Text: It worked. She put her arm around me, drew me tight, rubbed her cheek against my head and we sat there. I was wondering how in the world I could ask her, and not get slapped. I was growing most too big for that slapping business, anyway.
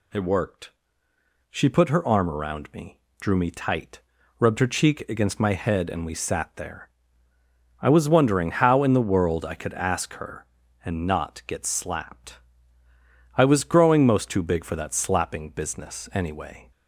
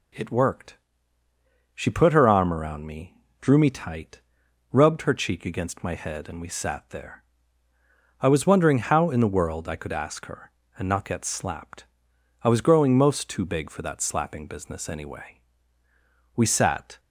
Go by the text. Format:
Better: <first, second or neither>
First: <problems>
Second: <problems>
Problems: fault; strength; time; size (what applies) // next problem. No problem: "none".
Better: first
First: none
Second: goes on to say "We sat"; noticeable; from 16.3 s on; 0.64 s long